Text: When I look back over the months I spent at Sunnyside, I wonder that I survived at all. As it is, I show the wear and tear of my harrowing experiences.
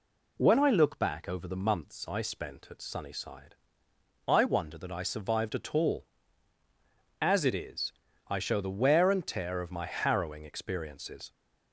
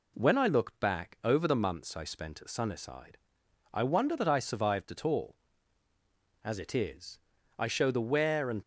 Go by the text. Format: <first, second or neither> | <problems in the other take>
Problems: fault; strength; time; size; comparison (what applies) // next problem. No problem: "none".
first | stops before "tear of my harrowing experiences"; at 8.6 s